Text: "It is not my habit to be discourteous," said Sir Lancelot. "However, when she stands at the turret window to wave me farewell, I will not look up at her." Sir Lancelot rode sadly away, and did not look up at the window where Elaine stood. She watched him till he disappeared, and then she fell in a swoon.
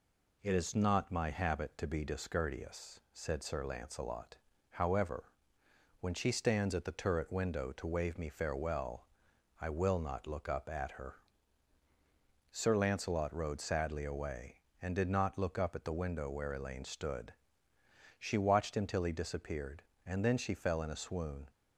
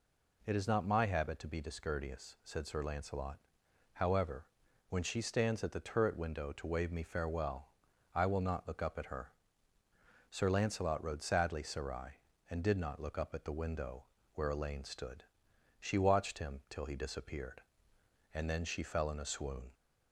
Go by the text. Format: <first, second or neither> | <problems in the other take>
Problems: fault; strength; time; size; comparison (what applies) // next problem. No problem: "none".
first | says "sarai" for "away"; at 11.6 s // pauses between "window" and "where"; slight; at 14.0 s; 0.28 s long